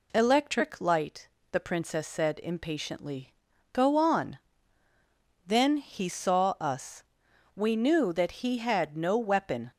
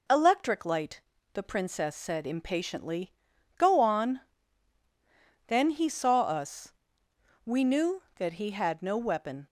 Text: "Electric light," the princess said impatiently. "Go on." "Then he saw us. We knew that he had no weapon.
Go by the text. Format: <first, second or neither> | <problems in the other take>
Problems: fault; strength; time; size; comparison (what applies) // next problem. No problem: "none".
neither | none